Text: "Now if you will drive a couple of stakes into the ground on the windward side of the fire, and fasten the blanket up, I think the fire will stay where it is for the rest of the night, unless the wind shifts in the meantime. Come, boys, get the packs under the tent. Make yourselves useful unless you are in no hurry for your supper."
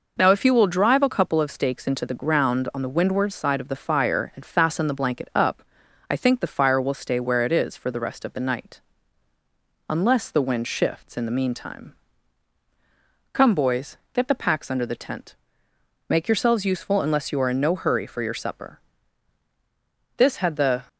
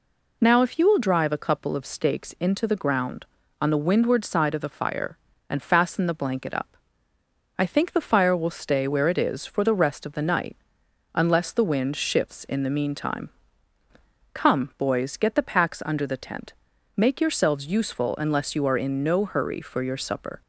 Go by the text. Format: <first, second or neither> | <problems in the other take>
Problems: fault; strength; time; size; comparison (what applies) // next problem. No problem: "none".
second | goes on to say "This had the"; noticeable; from 20.1 s on; 0.72 s long